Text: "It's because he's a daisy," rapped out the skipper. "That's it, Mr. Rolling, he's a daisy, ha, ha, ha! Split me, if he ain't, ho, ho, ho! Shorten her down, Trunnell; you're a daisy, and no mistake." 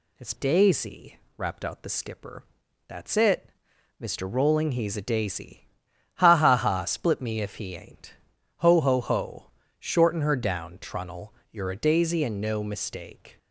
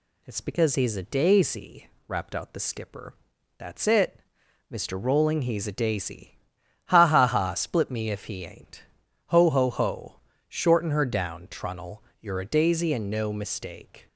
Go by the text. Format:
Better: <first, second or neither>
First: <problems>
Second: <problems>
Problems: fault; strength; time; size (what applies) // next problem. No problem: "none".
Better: second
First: skips "because he's a"; at 0.3 s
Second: none